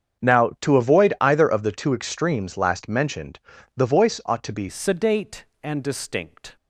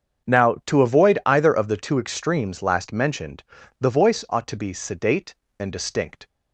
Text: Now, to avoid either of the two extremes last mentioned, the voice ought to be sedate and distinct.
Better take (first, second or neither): second